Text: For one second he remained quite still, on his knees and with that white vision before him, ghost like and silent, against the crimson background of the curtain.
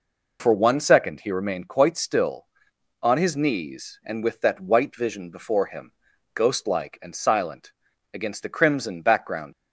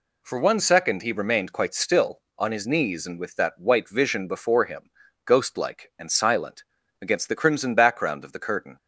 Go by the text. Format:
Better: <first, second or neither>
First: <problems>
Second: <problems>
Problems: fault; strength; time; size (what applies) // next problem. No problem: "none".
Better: second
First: stops before "of the curtain"; at 9.5 s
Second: none